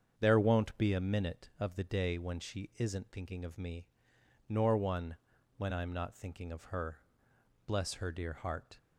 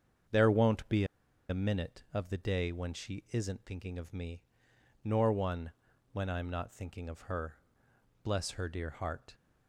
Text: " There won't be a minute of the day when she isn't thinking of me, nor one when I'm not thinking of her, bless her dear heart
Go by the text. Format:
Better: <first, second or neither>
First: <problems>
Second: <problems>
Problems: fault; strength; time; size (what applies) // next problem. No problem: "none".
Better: first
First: starts louder than the rest; strong; until 1.2 s; 7 dB // pauses between "one" and "when"; at 5.1 s; 0.40 s long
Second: starts louder than the rest; strong; until 1.7 s; 7 dB // pauses between "be" and "a"; at 1.0 s; 0.45 s long // pauses between "one" and "when"; at 5.7 s; 0.40 s long